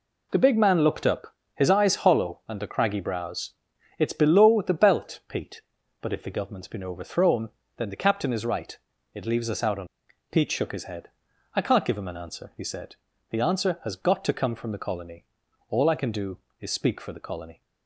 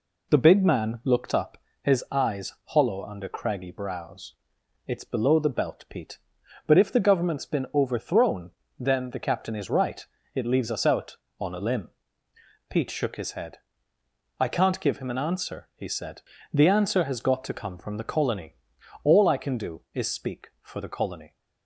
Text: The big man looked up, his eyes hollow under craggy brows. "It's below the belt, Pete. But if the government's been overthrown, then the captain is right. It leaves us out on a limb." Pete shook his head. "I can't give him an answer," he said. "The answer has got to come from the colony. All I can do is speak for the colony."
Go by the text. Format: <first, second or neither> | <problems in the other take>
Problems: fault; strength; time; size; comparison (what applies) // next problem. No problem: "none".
second | skips "a limb"; at 10.0 s